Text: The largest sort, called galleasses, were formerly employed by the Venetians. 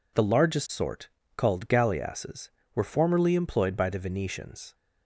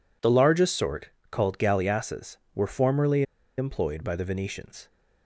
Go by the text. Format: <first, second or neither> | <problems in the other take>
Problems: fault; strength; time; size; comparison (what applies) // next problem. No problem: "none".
first | pauses between "formerly" and "employed"; slight; at 3.2 s; 0.34 s long